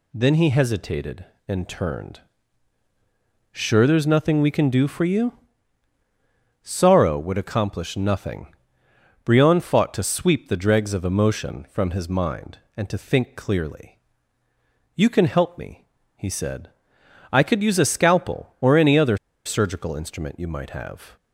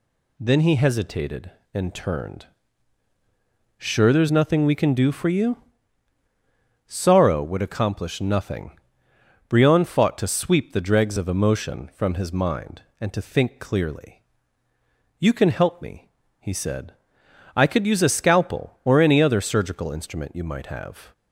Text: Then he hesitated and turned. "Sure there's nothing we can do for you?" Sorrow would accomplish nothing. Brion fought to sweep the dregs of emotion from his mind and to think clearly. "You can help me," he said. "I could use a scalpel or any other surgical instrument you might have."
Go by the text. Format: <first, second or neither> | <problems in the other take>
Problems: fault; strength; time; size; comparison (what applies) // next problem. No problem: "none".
second | pauses between "other" and "surgical"; slight; at 19.1 s; 0.27 s long